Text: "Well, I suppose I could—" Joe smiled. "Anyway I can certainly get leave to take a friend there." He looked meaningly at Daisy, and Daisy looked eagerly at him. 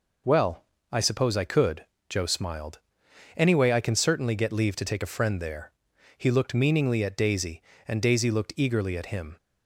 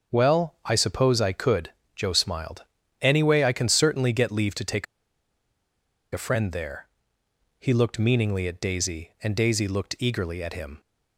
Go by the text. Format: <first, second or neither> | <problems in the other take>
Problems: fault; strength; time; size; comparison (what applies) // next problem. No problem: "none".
first | starts louder than the rest; noticeable; until 1.2 s; 6 dB // pauses between "take" and "a"; strong; at 4.8 s; 1.2 s long